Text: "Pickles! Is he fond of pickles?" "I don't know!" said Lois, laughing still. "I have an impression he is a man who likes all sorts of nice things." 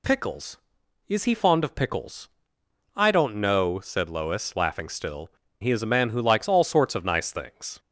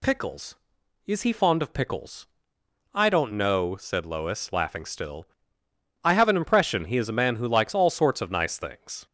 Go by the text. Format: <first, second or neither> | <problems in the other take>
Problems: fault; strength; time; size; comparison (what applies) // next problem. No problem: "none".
second | skips "I have an impression"; at 5.4 s